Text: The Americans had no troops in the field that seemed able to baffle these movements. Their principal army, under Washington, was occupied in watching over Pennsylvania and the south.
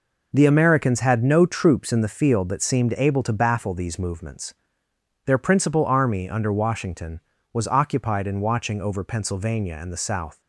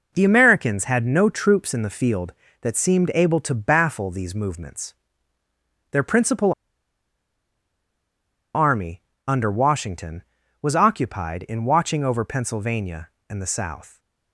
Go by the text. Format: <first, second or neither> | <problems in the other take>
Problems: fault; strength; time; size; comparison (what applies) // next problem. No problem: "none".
first | pauses between "principal" and "army"; strong; at 6.5 s; 2.0 s long